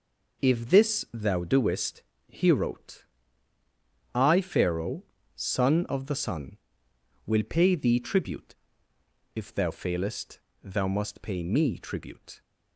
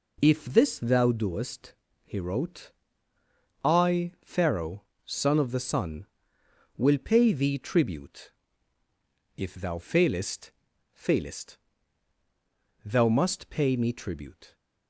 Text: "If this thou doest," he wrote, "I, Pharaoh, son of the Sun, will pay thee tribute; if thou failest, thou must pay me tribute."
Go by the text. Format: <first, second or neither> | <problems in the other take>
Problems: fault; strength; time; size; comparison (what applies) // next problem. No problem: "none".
first | says "failest" twice; at 10.9 s